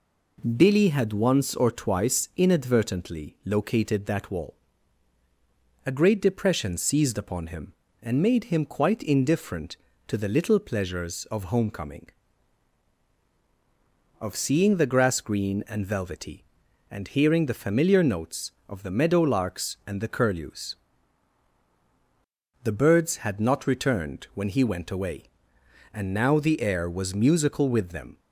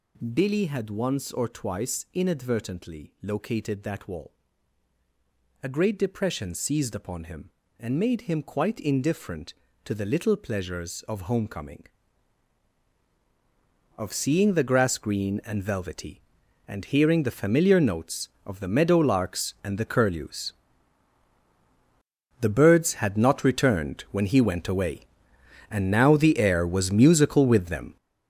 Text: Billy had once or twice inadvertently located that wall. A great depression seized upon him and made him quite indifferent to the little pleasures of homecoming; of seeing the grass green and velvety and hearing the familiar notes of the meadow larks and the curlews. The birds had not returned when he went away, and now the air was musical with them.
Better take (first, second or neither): first